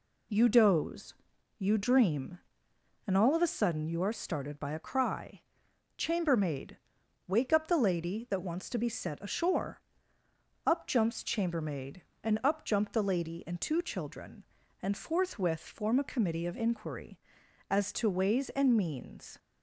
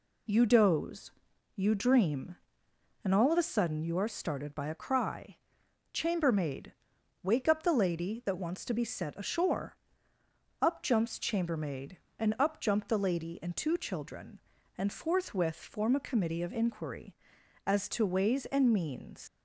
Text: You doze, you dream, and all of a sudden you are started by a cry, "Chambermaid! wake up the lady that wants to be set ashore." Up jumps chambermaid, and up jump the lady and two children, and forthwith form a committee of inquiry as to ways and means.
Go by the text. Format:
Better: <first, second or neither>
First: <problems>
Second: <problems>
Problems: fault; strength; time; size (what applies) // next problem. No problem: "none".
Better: first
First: none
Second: leaves "means" unfinished; at 19.2 s; 70 ms